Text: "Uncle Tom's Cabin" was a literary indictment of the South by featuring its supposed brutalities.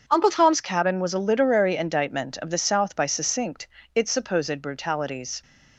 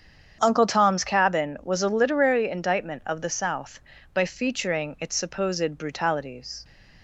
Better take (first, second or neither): second